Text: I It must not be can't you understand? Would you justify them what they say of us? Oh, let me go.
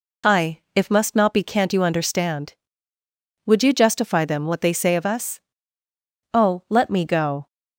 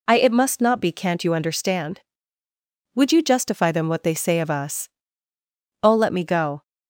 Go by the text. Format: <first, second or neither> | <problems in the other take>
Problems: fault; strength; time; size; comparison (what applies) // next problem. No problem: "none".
second | says "If" for "It"; at 0.7 s